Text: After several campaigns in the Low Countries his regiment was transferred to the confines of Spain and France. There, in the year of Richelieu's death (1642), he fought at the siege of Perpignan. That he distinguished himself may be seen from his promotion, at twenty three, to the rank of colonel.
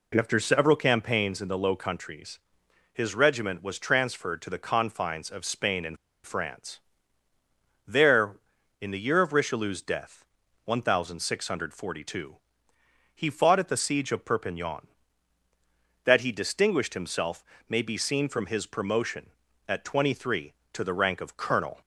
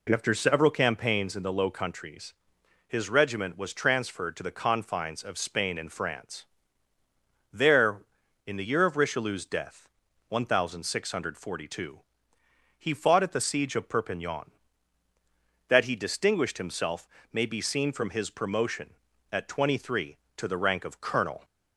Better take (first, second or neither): second